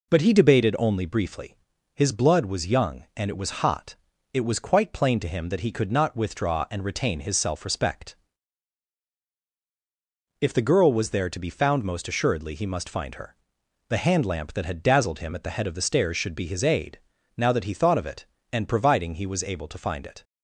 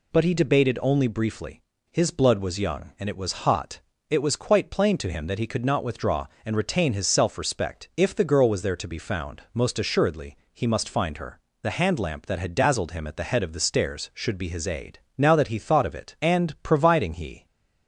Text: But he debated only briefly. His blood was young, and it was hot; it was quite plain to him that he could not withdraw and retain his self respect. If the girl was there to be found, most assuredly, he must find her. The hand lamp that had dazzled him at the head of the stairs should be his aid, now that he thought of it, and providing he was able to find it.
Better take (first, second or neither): first